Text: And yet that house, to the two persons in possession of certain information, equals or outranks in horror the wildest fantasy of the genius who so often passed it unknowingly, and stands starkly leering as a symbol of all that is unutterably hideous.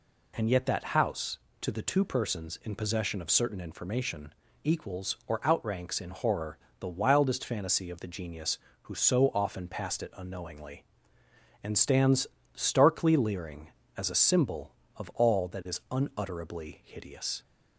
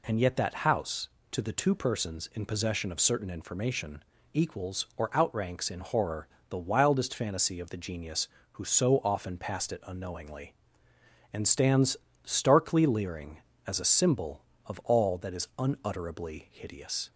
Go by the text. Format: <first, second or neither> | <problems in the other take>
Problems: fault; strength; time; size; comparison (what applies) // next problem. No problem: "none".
neither | pauses between "horror" and "the"; slight; the same in both // pauses between "stands" and "starkly"; slight; the same in both